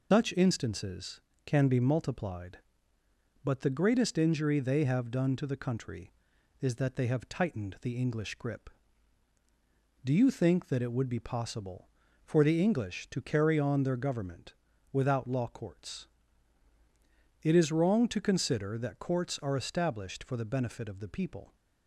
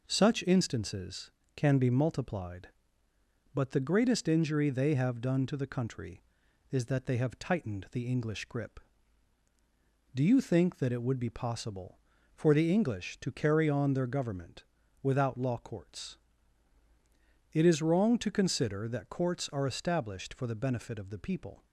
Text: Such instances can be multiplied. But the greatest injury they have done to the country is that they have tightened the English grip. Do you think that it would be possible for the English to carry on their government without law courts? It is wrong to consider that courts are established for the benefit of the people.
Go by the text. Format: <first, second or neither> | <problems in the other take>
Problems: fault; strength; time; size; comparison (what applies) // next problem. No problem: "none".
second | loses the start of "Such"; at 0.1 s; 155 ms // pauses between "government" and "without"; at 14.5 s; 0.38 s long; also in the second